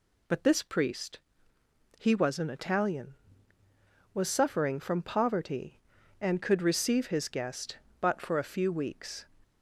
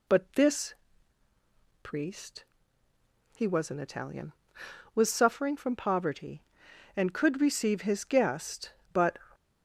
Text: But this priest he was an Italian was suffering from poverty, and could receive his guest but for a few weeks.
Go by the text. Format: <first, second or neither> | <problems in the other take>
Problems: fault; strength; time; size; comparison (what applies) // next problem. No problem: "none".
first | pauses between "this" and "priest"; at 0.7 s; 1.0 s long // pauses between "priest" and "he"; noticeable; at 2.4 s; 0.92 s long; noticeable in the first // stops before "for a few weeks"; at 9.3 s